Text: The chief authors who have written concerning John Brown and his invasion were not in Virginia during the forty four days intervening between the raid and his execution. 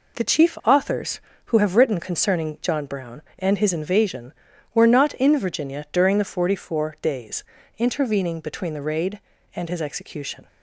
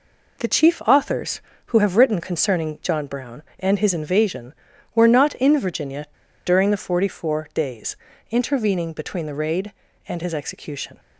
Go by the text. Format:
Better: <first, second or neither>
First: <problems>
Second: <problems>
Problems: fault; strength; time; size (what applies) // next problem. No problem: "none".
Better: first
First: pauses between "days" and "intervening"; slight; at 7.4 s; 0.34 s long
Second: pauses between "Virginia" and "during"; at 6.0 s; 0.40 s long // pauses between "days" and "intervening"; slight; at 7.9 s; 0.34 s long